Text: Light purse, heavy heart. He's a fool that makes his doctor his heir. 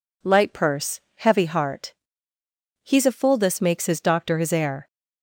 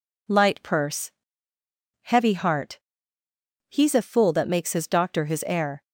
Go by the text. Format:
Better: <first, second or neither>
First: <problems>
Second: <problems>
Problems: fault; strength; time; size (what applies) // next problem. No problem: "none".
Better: second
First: says "this" for "that"; at 3.3 s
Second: none